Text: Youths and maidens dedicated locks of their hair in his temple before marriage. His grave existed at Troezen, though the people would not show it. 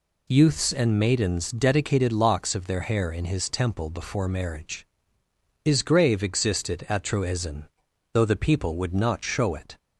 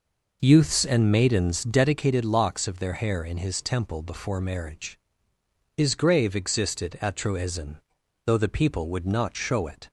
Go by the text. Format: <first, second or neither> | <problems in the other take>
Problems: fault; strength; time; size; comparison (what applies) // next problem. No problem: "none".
first | starts louder than the rest; noticeable; until 1.9 s; 5 dB